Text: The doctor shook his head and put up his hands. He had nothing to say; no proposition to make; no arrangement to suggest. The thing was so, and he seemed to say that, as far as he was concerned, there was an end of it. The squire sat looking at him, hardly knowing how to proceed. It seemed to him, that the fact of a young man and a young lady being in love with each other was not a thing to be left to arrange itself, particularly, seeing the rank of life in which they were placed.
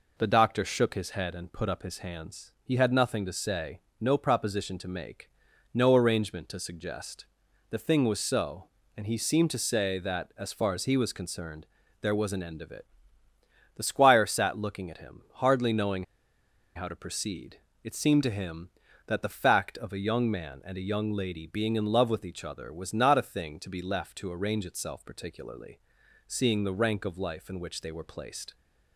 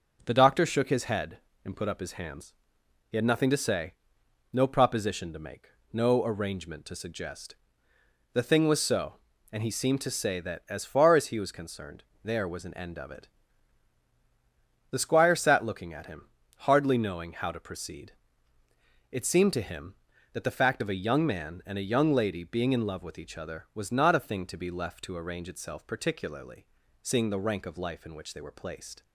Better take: second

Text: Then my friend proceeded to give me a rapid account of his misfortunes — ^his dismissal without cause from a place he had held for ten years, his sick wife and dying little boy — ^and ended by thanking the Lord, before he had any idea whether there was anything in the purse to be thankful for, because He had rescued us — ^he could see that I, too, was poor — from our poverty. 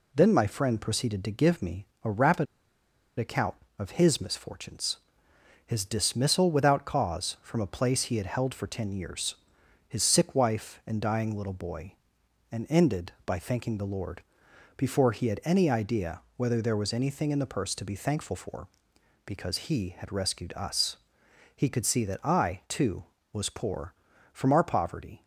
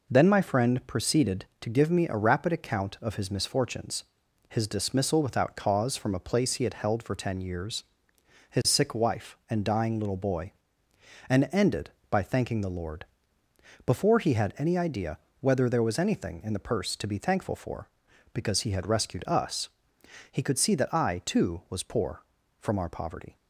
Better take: second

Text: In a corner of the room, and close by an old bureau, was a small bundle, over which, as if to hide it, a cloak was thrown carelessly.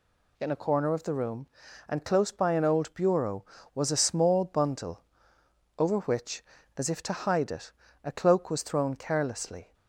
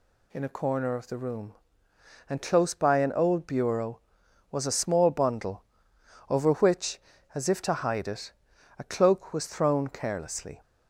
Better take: neither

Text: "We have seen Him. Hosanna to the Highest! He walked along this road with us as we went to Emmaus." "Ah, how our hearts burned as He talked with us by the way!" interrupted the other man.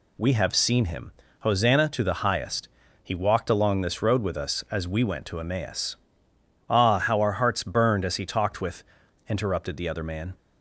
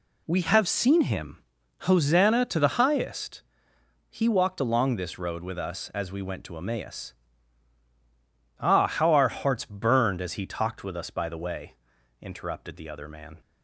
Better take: second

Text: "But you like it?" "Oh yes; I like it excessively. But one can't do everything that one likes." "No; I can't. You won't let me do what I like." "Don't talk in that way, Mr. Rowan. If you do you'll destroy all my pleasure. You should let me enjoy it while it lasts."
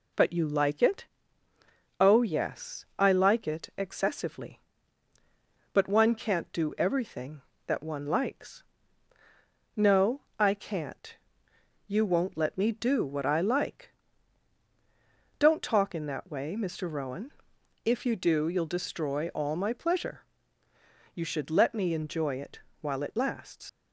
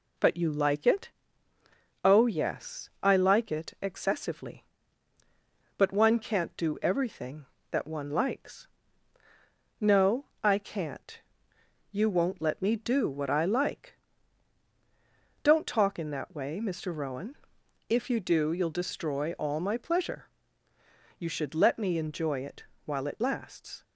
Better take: second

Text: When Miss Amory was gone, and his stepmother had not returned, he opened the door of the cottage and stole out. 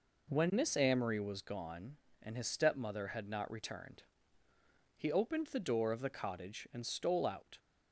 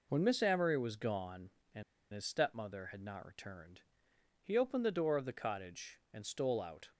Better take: first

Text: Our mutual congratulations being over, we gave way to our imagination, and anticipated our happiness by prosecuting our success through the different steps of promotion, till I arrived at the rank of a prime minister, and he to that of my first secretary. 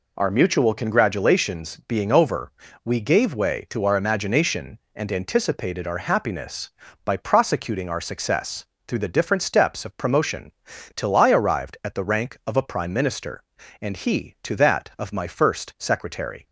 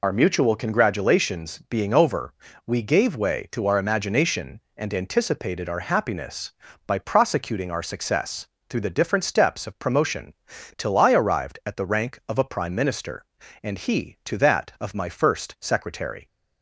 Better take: first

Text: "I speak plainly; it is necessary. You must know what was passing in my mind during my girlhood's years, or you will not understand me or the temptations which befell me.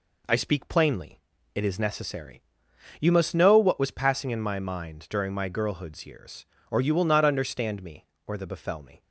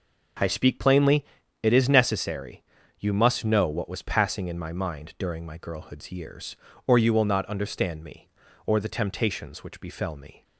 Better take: second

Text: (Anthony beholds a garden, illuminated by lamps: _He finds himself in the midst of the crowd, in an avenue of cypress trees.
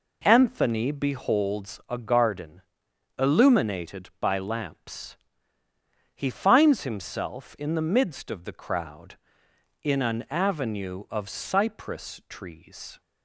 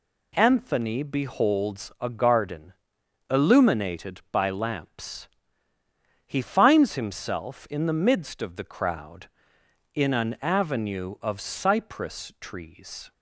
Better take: second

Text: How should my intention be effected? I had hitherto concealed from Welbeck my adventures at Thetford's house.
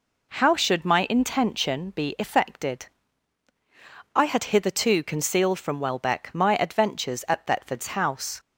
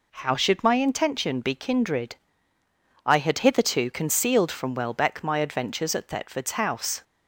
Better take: first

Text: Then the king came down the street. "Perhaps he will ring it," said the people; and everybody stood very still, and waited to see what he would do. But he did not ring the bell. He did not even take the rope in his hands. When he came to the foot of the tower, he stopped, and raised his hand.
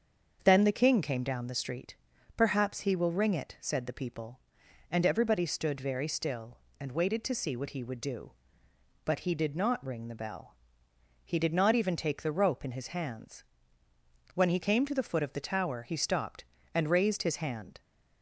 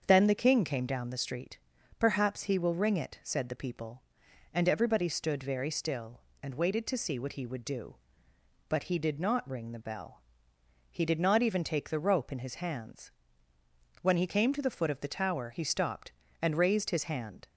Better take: neither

